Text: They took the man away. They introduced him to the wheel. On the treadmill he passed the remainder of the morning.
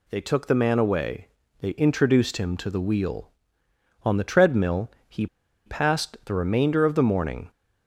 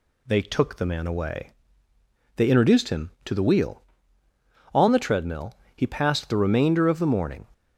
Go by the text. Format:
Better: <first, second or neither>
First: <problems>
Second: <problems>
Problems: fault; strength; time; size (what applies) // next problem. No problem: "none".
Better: second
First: pauses between "treadmill" and "he"; slight; at 4.8 s; 0.20 s long // pauses between "he" and "passed"; at 5.2 s; 0.39 s long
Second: pauses between "treadmill" and "he"; slight; at 5.5 s; 0.20 s long